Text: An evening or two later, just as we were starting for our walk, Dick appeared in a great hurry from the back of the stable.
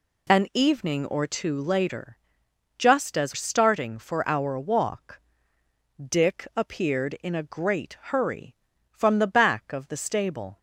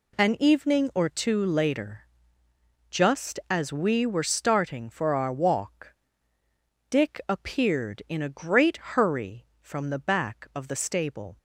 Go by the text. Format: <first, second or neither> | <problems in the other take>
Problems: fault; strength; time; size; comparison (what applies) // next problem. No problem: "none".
second | skips "we were"; at 3.3 s